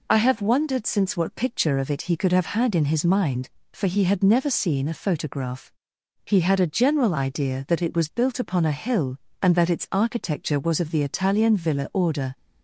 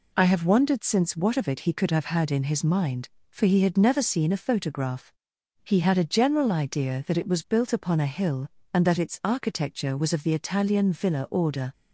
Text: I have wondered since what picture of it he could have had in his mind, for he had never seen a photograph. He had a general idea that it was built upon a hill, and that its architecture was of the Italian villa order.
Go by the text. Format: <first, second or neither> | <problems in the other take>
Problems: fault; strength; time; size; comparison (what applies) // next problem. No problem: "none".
first | skips "picture"; at 1.3 s